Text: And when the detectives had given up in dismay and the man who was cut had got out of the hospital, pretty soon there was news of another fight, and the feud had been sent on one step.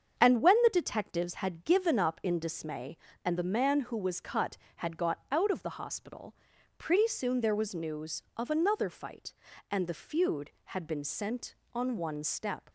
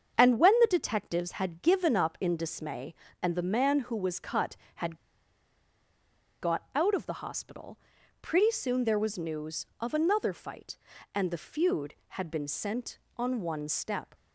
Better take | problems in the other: first | starts louder than the rest; until 1.2 s; 7 dB; also in the first // pauses between "had" and "got"; strong; at 4.9 s; 1.4 s long

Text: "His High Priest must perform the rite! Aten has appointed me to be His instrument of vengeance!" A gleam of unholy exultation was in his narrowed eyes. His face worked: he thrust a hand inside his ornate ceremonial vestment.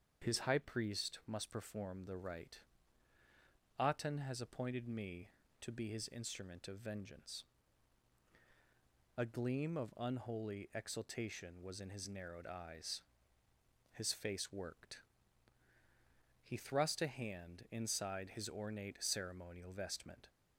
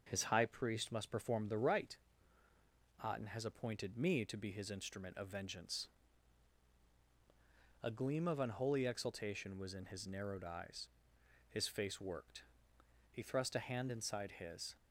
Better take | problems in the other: first | starts louder than the rest; noticeable; until 1.0 s; 6 dB; also in the first // stops before "ornate ceremonial vestment"; at 14.7 s

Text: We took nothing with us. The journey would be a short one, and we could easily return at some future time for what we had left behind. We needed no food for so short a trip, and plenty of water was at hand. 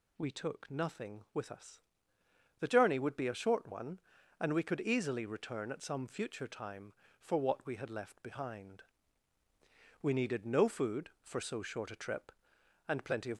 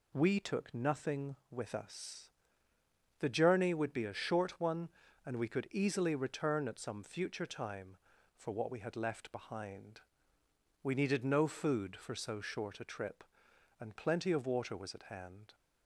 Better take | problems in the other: second | stops before "water was at hand"; at 13.3 s

